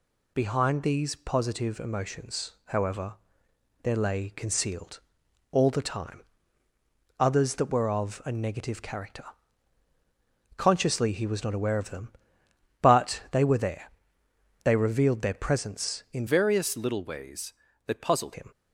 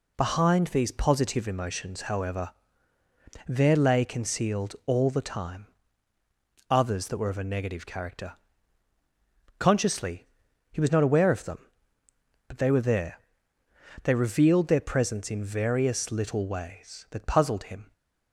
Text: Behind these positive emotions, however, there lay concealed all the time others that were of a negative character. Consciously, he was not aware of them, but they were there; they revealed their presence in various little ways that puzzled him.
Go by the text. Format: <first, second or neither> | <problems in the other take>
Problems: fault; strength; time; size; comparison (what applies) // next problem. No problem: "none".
second | pauses between "concealed" and "all"; noticeable; at 4.9 s; 0.52 s long // pauses between "time" and "others"; noticeable; at 6.2 s; 0.96 s long; also in the second // changes voice from "various" to "puzzled"; from 16.2 to 18.3 s; 2.1 s long